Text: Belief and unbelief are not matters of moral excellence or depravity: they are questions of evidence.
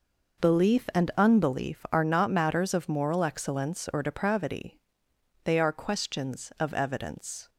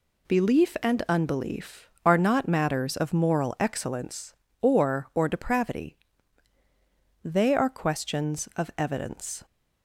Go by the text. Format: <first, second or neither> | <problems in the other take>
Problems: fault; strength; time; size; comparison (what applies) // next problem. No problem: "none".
first | says "or" twice; at 5.1 s